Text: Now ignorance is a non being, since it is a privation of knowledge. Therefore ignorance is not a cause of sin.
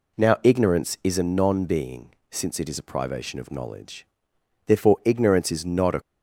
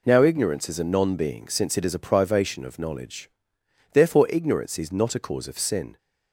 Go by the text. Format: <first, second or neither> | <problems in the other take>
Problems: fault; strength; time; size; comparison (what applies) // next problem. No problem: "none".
second | stops before "cause of sin"; at 6.0 s